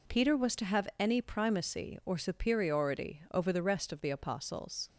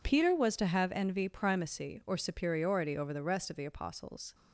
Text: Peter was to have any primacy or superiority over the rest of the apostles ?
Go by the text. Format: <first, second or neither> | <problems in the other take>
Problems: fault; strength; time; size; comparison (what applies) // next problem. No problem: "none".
first | says "envy" for "any"; at 0.9 s